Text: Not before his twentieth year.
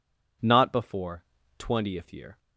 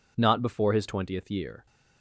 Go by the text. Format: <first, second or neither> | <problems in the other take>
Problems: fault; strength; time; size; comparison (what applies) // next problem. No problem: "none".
second | skips "his"; at 1.4 s